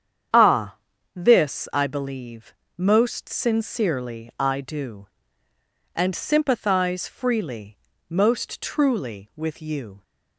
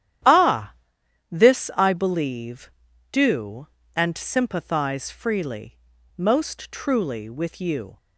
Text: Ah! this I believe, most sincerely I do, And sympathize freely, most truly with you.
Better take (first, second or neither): first